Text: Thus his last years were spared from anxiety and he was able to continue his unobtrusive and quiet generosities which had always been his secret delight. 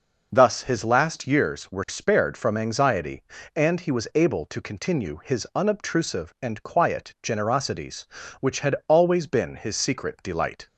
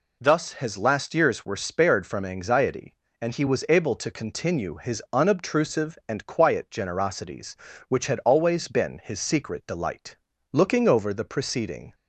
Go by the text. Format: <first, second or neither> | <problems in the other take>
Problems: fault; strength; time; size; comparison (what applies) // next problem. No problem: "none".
first | goes on to say "Looking over the preceding"; from 10.5 s on; 1.4 s long